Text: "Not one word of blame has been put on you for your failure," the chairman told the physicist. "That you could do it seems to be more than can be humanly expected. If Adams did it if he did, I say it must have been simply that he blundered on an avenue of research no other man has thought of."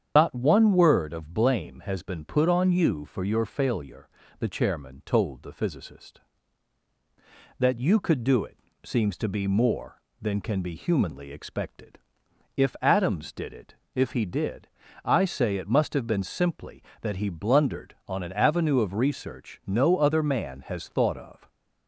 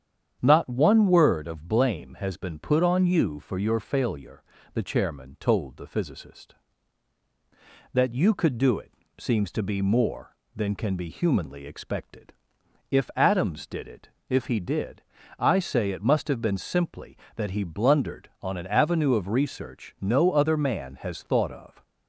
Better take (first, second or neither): second